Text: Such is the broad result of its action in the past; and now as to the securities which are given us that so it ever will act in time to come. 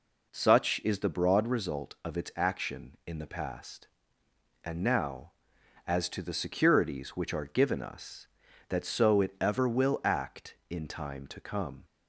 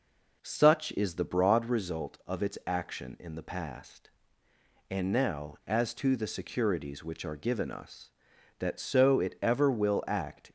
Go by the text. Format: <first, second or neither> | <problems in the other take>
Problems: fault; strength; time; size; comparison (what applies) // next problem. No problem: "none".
first | stops before "in time to come"; at 10.4 s